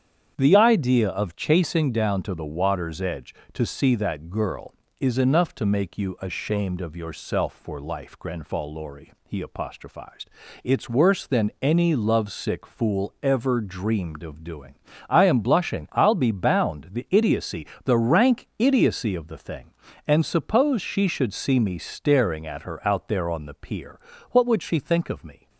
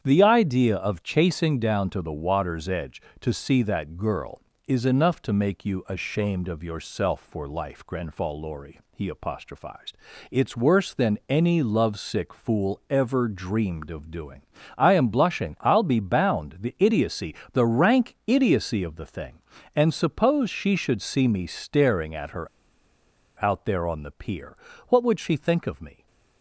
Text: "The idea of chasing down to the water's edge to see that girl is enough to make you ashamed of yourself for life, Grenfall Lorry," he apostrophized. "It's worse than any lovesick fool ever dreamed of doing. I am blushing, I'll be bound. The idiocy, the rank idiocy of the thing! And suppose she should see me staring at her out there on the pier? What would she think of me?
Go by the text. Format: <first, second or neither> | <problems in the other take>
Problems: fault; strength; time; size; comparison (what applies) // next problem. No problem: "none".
first | starts louder than the rest; strong; until 1.0 s; 8.5 dB; strong in the first // pauses between "her" and "out"; noticeable; at 22.4 s; 0.96 s long